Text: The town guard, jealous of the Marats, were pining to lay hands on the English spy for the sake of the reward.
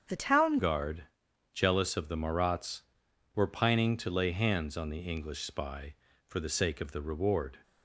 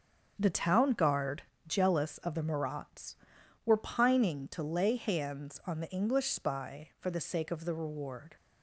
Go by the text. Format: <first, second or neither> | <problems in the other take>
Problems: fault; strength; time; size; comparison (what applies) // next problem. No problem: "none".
second | starts louder than the rest; strong; until 1.5 s; 7.5 dB; also in the second // changes voice at "guard"; from 0.5 s on; 7.0 s long